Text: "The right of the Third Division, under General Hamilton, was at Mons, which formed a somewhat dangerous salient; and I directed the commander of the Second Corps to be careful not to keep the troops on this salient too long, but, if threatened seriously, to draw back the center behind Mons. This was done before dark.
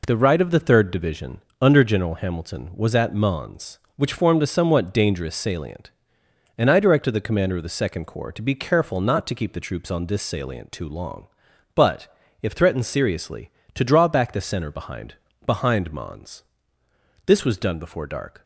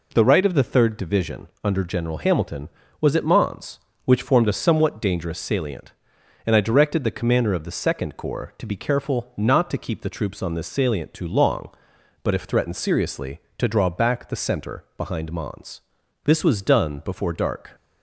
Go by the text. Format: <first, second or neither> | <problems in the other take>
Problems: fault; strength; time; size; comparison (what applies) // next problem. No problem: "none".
second | says "behind" twice; at 15.4 s